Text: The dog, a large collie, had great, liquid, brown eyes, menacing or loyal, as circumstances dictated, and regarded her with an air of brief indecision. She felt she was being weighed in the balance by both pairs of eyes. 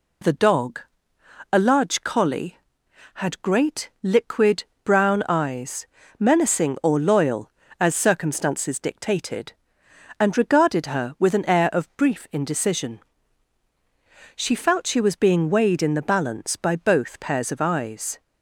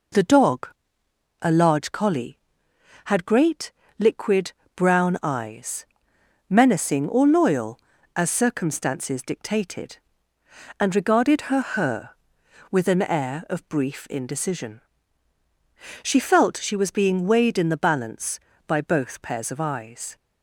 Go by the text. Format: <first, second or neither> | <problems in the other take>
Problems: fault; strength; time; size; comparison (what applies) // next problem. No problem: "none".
first | says "her" twice; at 11.6 s